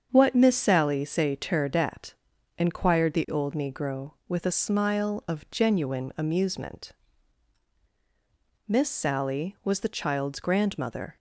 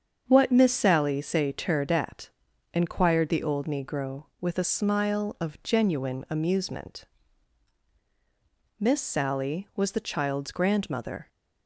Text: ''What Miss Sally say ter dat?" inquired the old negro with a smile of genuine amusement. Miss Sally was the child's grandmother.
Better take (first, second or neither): neither